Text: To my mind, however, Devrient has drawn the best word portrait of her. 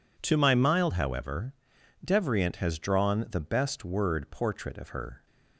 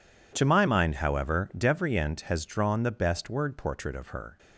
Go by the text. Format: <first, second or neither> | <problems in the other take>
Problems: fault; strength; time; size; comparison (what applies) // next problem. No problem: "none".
second | says "mild" for "mind"; at 0.5 s